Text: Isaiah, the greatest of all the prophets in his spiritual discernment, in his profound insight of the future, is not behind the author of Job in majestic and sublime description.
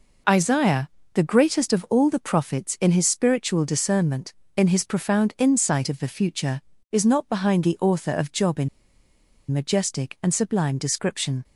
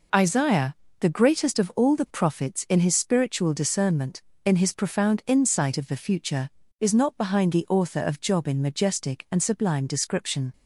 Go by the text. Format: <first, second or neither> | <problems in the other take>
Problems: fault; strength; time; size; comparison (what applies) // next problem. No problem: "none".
second | pauses between "in" and "majestic"; noticeable; at 8.6 s; 0.82 s long